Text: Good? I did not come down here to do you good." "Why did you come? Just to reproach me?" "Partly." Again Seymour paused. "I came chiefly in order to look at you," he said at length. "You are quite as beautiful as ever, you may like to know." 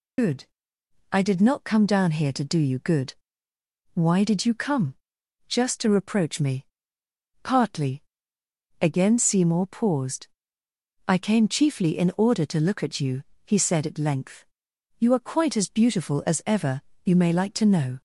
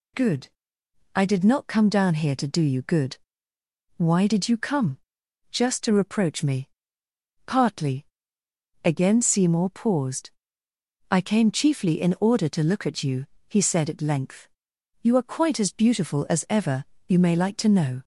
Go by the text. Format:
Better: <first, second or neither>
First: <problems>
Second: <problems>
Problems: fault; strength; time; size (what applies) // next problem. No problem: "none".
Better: second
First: loses the start of "Good"; at 0.1 s; 55 ms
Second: none